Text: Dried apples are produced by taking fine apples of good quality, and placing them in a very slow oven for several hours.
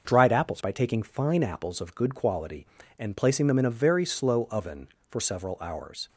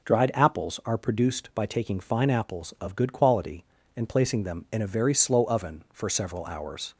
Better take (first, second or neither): second